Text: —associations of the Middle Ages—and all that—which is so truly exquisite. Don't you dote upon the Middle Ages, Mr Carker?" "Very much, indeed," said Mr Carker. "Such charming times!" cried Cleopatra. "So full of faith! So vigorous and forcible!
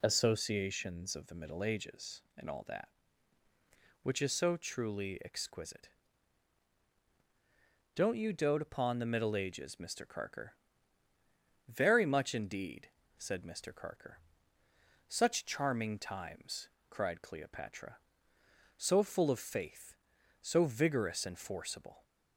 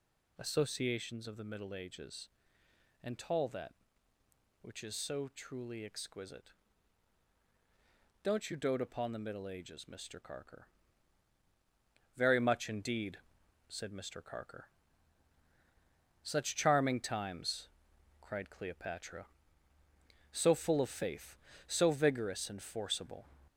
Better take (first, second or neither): first